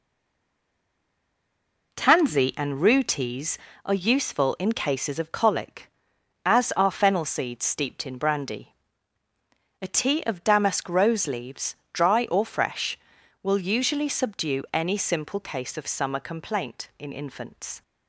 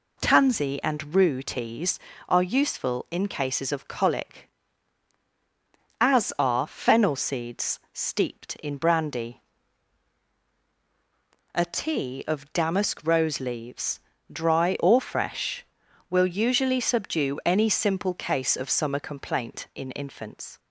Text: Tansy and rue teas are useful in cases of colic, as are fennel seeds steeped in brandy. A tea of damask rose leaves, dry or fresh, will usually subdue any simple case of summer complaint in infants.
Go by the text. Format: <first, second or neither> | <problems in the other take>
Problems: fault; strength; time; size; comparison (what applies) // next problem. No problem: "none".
second | stays silent before the first word; noticeable; until 1.9 s; 1.9 s long